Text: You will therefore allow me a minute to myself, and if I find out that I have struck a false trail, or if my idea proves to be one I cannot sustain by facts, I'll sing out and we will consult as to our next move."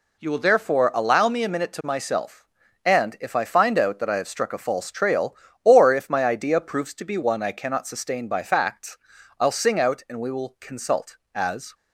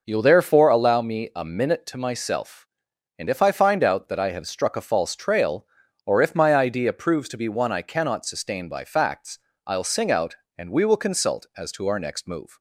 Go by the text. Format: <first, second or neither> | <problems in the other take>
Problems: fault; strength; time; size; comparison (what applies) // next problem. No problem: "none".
second | stops before "to our next move"; at 11.7 s